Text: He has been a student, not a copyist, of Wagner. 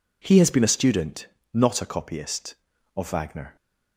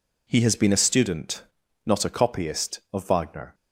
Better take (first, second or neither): neither